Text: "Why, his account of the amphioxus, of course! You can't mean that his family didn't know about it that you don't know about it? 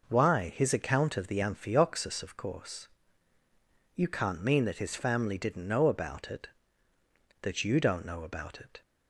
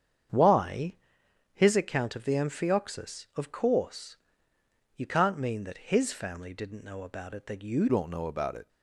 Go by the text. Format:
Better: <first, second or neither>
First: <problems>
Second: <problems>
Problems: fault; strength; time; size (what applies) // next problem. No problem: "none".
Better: first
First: none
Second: starts louder than the rest; strong; until 1.8 s; 8 dB // changes voice at "don't"; from 7.8 s on; 0.8 s long